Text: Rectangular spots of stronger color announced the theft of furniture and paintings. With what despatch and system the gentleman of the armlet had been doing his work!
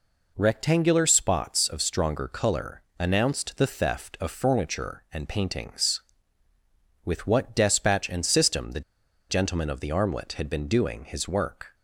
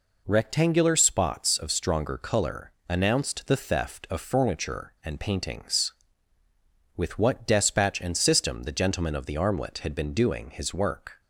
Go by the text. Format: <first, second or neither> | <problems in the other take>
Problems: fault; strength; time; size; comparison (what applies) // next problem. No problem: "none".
second | pauses between "color" and "announced"; slight; at 2.8 s; 0.18 s long; slight in the second // pauses between "the" and "gentleman"; noticeable; at 8.8 s; 0.48 s long